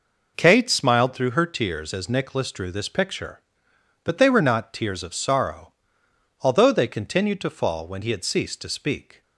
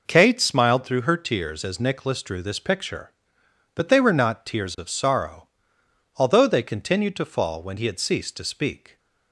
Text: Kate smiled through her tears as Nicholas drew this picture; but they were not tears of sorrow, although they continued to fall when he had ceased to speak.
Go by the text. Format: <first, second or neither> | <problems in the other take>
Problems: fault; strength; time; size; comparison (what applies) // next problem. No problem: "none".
neither | none